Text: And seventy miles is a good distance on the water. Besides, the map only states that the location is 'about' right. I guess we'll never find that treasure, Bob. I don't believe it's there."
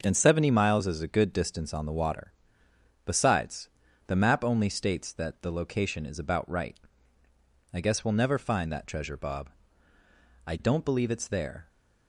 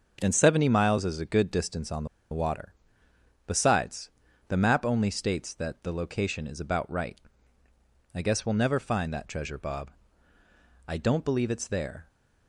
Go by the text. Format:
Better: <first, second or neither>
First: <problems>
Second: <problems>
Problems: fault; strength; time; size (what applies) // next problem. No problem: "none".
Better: first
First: starts louder than the rest; until 1.0 s; 6 dB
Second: starts louder than the rest; until 1.2 s; 6 dB // pauses between "the" and "water"; slight; at 2.0 s; 0.24 s long